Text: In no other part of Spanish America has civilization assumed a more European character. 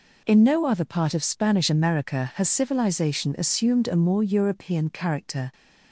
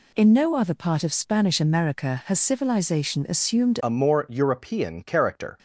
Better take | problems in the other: first | changes voice at "a"; from 3.8 s on; 1.7 s long

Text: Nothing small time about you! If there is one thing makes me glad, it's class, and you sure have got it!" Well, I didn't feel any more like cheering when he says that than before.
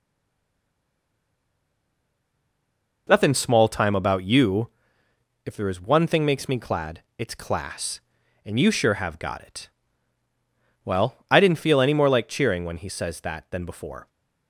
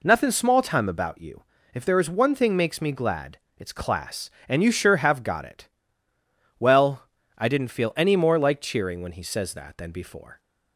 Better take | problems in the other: second | stays silent before the first word; strong; until 3.0 s; 3.0 s long

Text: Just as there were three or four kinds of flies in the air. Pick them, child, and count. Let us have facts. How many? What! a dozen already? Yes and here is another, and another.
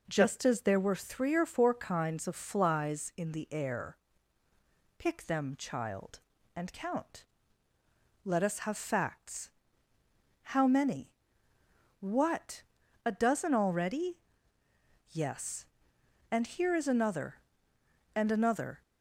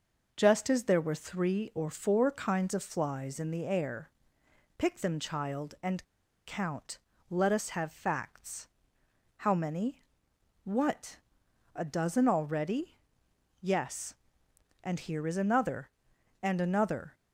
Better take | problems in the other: first | pauses between "and" and "count"; at 6.0 s; 0.43 s long

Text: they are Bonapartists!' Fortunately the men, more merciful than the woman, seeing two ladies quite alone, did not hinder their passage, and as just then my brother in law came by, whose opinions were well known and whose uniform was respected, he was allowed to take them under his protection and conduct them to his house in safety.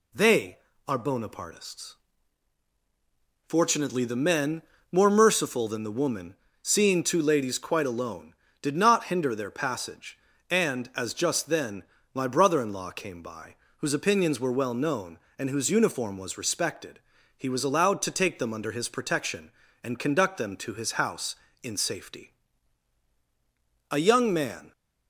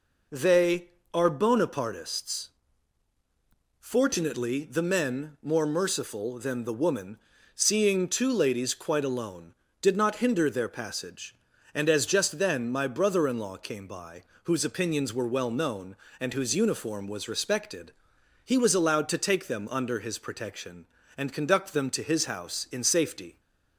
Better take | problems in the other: second | pauses between "then" and "my"; slight; at 11.8 s; 0.28 s long // goes on to say "A young man"; noticeable; from 23.9 s on; 0.80 s long

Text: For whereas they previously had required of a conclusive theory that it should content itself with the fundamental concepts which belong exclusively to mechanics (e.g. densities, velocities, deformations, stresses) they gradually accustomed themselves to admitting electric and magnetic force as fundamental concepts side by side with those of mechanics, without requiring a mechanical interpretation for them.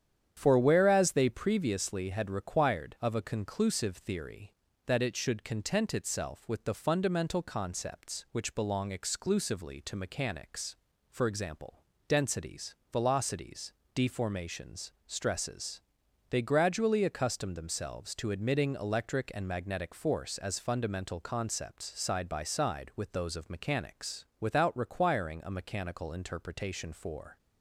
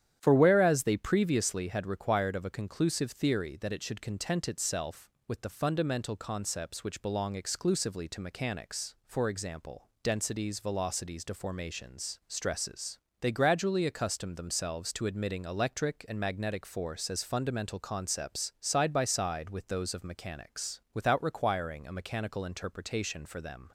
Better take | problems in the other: second | starts louder than the rest; strong; until 1.3 s; 9 dB; strong in the second // stops before "them"; at 27.3 s

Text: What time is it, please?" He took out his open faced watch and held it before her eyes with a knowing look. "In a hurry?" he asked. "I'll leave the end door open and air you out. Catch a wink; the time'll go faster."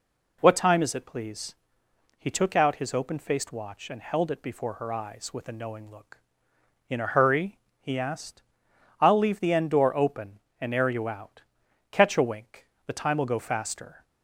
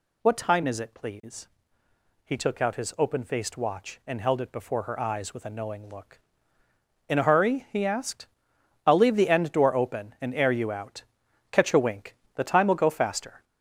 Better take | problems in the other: first | gets louder; noticeable; throughout; 5 dB

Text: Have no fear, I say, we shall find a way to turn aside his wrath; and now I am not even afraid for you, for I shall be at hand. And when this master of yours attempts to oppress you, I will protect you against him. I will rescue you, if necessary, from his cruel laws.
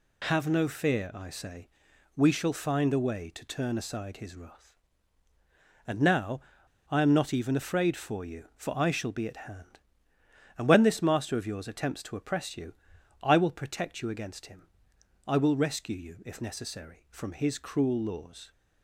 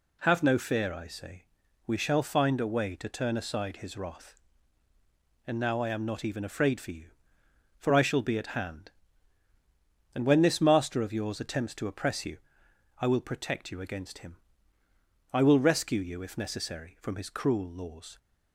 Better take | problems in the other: second | pauses between "now" and "I"; noticeable; at 6.3 s; 0.51 s long

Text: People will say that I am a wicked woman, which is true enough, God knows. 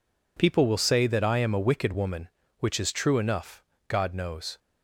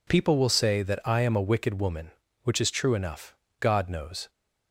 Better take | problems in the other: neither | none

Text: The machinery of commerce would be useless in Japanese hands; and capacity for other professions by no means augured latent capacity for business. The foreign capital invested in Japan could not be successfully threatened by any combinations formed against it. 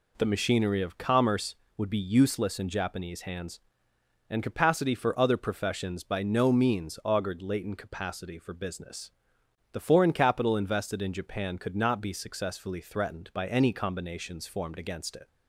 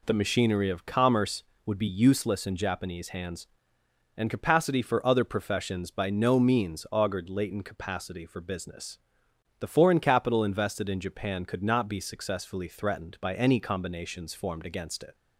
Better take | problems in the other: neither | none

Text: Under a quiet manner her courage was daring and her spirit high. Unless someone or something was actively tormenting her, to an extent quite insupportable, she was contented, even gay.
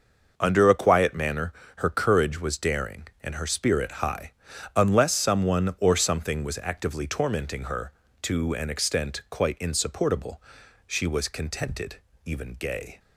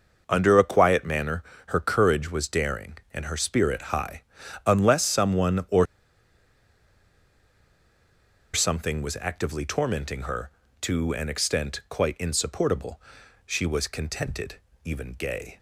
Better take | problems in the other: first | pauses between "manner" and "her"; slight; at 1.4 s; 0.24 s long; slight in the first // pauses between "or" and "something"; strong; at 5.8 s; 2.6 s long

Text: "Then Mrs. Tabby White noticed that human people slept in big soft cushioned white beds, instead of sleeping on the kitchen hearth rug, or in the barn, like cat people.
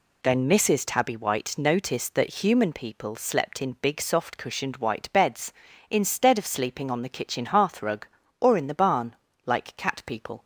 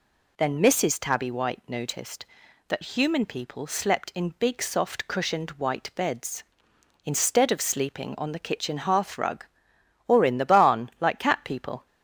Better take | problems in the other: neither | none

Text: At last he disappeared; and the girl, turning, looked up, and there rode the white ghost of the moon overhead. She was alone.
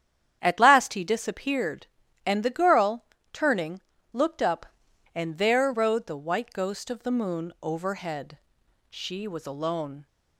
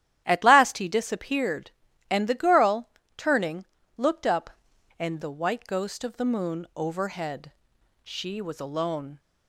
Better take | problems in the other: first | starts louder than the rest; strong; until 1.2 s; 11.5 dB; strong in the first // skips "there rode"; at 5.2 s

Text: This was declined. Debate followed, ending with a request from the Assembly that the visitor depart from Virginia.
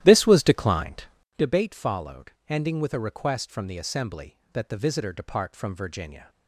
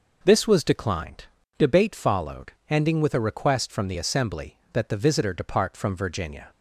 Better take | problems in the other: second | starts louder than the rest; strong; until 1.5 s; 13 dB

